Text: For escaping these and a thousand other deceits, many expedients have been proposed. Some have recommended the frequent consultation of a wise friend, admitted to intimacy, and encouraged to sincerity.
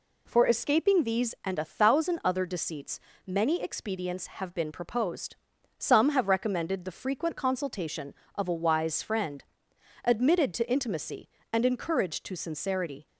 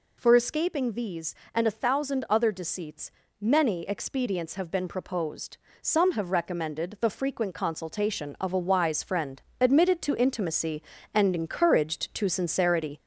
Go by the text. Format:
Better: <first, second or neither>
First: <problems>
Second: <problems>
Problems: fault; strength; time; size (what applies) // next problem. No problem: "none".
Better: first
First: none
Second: gets louder; slight; throughout; 3 dB